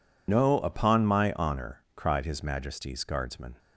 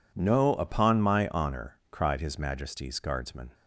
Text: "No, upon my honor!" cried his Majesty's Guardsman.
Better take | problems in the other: second | loses the start of "No"; at 0.2 s; 90 ms

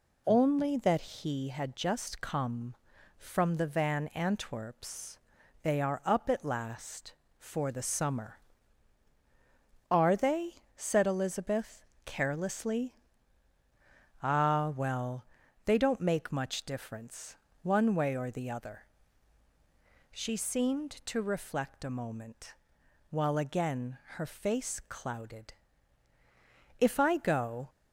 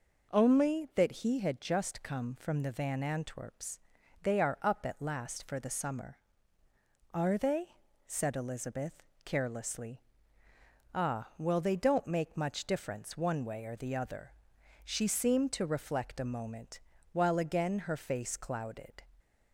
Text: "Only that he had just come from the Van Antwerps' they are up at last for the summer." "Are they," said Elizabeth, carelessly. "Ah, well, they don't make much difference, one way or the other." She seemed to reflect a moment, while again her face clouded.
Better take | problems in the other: second | pauses between "Antwerps" and "they"; at 5.1 s; 0.42 s long; also in the second // pauses between "again" and "her"; slight; at 23.9 s; 0.16 s long // goes on to say "If I go"; noticeable; from 26.7 s on; 0.90 s long

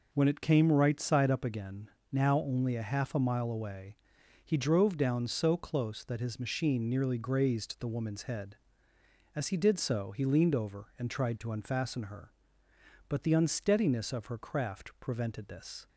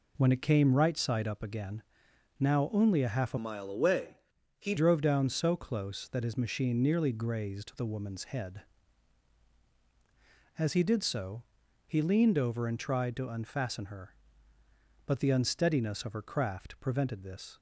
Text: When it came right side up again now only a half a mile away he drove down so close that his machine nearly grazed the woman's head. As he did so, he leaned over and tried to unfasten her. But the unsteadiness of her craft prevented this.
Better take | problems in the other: first | pauses between "again" and "now"; noticeable; at 1.8 s; 0.56 s long; slight in the first // changes voice from "mile" to "he"; from 3.3 to 4.7 s; 1.4 s long // pauses between "away" and "he"; at 4.1 s; 0.42 s long; noticeable in the first

